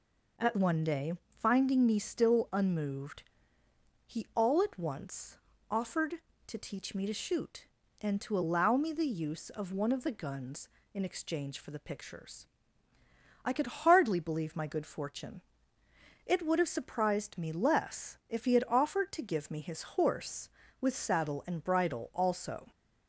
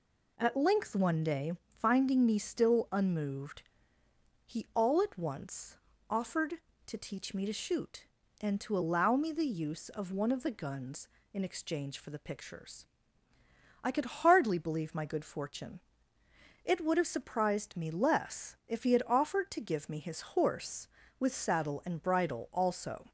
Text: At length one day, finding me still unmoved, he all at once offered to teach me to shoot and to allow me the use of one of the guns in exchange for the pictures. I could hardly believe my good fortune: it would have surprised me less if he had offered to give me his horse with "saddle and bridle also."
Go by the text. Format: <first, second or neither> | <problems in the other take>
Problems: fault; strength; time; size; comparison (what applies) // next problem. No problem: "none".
second | skips "length"; at 0.5 s // pauses between "once" and "offered"; slight; at 5.3 s; 0.32 s long; slight in the second